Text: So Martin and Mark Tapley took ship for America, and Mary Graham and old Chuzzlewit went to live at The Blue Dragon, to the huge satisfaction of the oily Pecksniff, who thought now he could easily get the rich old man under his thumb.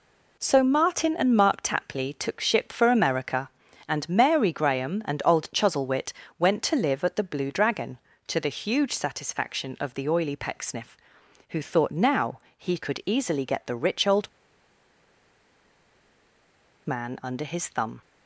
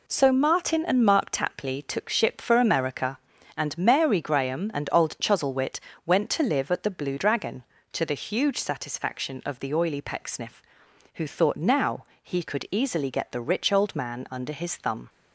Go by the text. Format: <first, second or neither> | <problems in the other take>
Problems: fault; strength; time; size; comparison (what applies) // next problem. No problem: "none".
second | pauses between "Chuzzlewit" and "went"; slight; at 6.1 s; 0.26 s long; slight in the second // pauses between "now" and "he"; slight; at 12.3 s; 0.16 s long; slight in the second // pauses between "old" and "man"; strong; at 14.2 s; 2.5 s long